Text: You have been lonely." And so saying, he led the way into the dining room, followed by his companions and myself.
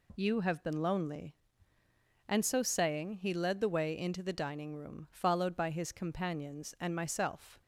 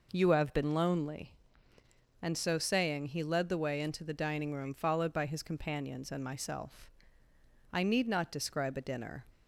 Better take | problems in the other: first | goes on to say "I need not describe a dinner"; from 7.7 s on; 1.5 s long

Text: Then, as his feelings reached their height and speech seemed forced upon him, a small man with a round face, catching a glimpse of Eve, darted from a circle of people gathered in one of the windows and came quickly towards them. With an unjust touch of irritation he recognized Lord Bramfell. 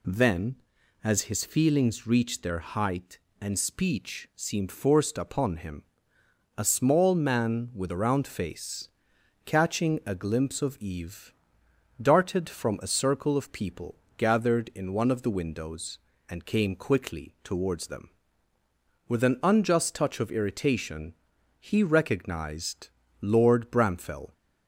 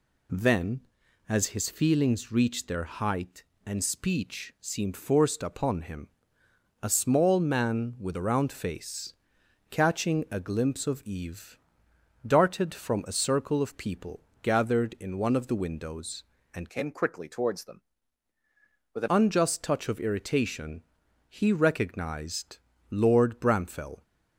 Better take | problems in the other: first | pauses between "people" and "gathered"; slight; at 14.2 s; 0.22 s long; slight in the first // changes voice from "came" to "an"; from 16.6 to 19.0 s; 2.4 s long // pauses between "irritation" and "he"; noticeable; at 20.8 s; 0.46 s long; also in the first // pauses between "recognized" and "Lord"; slight; at 22.5 s; 0.32 s long; slight in the first

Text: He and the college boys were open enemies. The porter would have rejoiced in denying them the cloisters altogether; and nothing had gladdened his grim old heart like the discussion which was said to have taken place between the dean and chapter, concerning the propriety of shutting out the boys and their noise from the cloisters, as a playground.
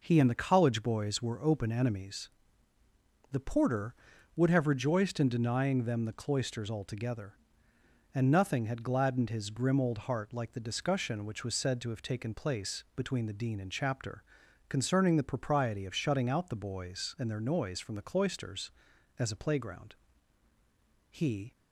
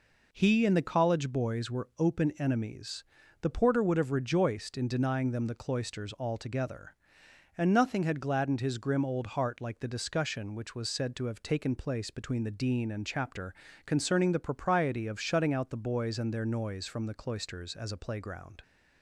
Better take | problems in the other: second | goes on to say "He"; slight; from 21.1 s on; 0.44 s long

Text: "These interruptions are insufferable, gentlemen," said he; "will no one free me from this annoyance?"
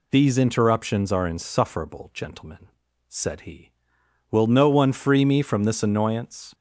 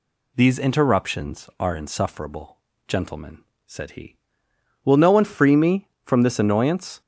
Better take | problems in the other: neither | none

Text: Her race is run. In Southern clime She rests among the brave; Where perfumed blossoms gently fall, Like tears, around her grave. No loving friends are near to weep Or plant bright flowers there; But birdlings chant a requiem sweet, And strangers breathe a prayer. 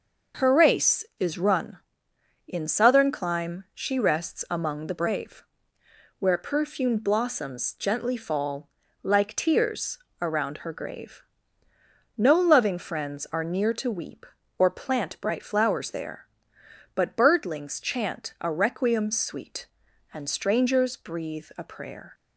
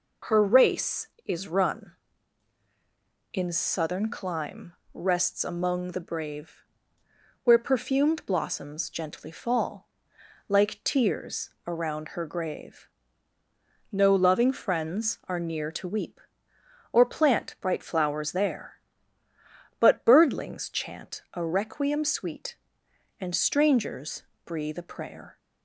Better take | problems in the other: first | skips "She"; at 4.8 s // pauses between "strangers" and "breathe"; slight; at 24.2 s; 0.22 s long

